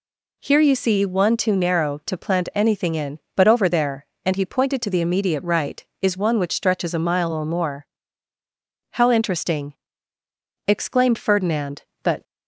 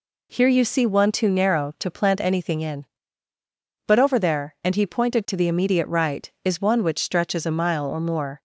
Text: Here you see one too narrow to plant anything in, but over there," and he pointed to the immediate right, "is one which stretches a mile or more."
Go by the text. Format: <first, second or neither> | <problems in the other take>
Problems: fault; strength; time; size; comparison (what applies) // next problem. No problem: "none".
second | goes on to say "How interesting exclaimed Ferdinand But"; strong; from 8.9 s on; 3.3 s long